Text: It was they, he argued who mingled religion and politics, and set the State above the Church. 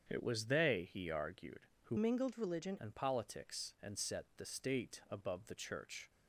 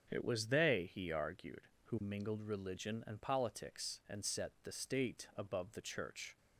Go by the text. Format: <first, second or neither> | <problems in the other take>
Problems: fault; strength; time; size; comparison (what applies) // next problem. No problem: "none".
second | starts louder than the rest; strong; until 1.1 s; 7.5 dB; also in the second // changes voice from "mingled" to "religion"; from 1.9 to 2.7 s; 0.8 s long